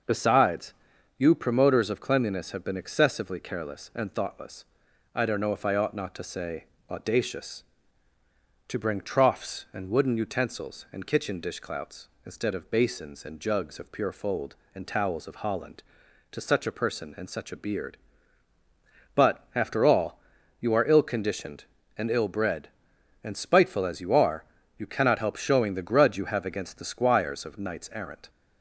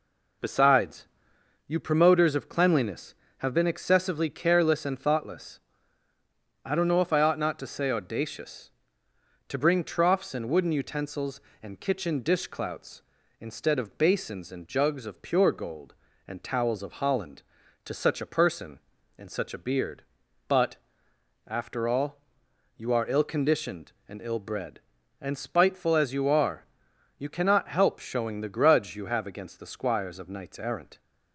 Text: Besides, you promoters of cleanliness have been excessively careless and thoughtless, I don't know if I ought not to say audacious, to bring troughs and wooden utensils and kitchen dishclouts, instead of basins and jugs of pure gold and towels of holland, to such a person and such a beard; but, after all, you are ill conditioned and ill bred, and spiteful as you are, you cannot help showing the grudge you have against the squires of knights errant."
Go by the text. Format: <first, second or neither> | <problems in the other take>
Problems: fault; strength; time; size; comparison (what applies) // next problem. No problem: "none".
second | pauses between "say" and "audacious"; slight; at 6.6 s; 0.26 s long // says "fold" for "gold"; at 14.1 s